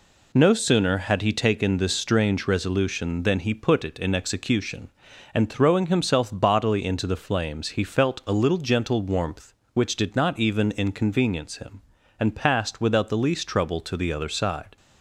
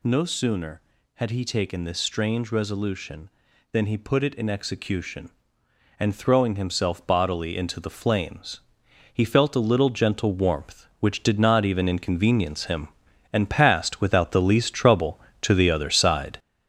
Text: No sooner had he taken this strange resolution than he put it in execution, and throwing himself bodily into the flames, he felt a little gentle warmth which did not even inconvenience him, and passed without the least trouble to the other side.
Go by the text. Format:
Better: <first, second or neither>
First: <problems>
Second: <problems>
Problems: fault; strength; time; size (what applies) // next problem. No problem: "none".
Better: first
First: none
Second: gets louder; throughout; 6.5 dB